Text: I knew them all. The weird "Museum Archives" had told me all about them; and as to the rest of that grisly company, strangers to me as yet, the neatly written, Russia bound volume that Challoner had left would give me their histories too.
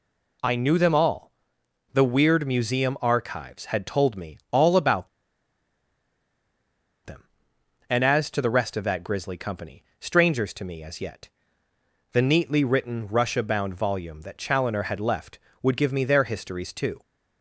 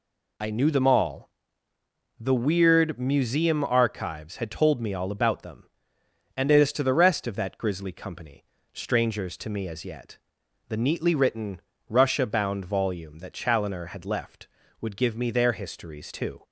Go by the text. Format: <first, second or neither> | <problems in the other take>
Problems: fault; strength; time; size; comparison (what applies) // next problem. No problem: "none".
second | pauses between "about" and "them"; strong; at 5.0 s; 1.9 s long